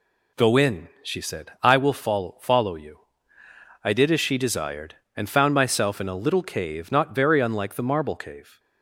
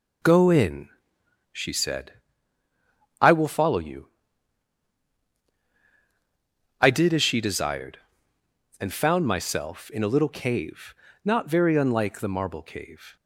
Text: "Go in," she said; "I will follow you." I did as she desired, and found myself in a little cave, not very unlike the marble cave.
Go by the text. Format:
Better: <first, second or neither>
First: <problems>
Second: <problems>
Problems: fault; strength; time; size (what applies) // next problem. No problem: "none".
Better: second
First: says "follow" twice; at 2.4 s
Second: none